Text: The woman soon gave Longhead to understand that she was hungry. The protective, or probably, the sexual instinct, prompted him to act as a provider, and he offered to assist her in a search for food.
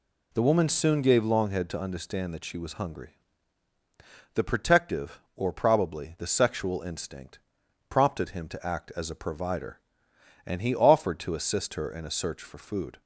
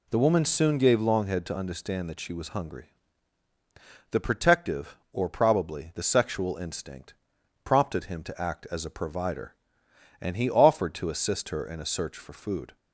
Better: neither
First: none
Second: none

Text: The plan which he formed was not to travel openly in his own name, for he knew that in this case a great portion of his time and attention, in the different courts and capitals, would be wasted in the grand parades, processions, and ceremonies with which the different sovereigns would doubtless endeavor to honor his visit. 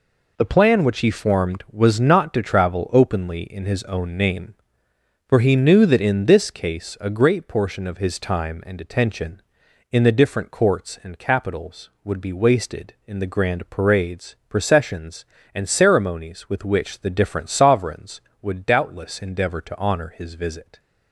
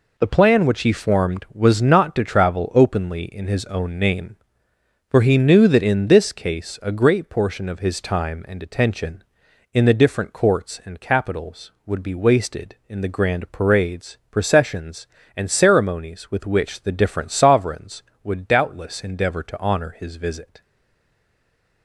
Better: first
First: none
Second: stays silent after the last word; noticeable; from 20.6 s on; 1.2 s long

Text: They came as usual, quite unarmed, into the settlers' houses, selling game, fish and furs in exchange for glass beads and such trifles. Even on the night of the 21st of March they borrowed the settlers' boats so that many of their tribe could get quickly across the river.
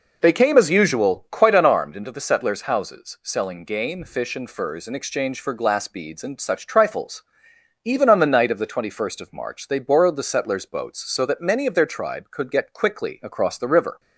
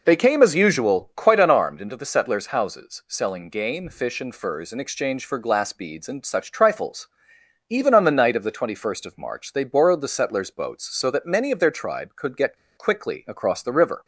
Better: first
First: none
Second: pauses between "get" and "quickly"; slight; at 12.5 s; 0.20 s long

